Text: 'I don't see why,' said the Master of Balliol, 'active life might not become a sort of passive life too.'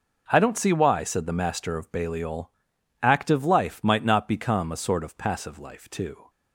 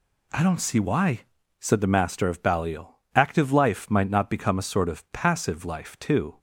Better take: neither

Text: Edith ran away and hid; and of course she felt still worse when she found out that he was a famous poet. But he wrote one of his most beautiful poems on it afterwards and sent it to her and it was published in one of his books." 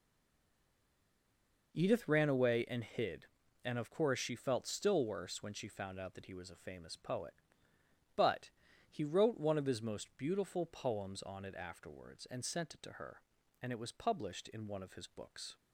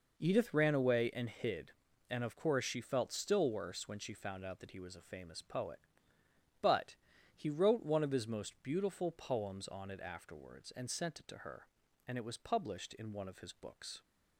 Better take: second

